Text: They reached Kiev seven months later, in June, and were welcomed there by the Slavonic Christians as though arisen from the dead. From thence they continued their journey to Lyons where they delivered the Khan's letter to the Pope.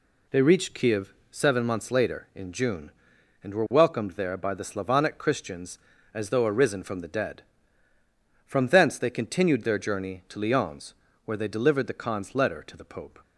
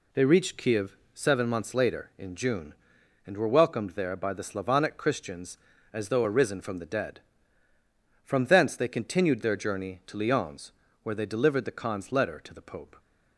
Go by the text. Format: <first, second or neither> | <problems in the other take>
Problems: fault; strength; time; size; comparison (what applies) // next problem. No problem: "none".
neither | pauses between "Kiev" and "seven"; slight; the same in both // pauses between "Lyons" and "where"; slight; the same in both